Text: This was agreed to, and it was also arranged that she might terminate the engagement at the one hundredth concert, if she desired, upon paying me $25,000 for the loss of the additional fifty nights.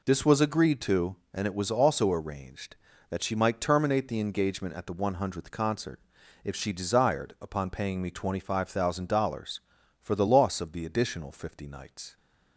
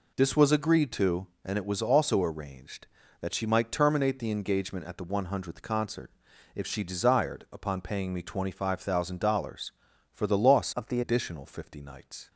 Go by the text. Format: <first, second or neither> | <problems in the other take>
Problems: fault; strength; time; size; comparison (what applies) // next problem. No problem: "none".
first | changes voice from "of" to "the"; from 10.7 to 11.0 s; 0.3 s long